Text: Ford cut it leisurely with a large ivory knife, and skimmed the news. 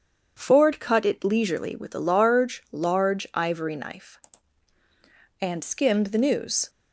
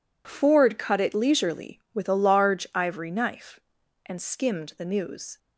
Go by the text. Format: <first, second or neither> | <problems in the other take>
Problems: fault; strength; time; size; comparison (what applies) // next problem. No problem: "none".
second | says "large" twice; at 2.7 s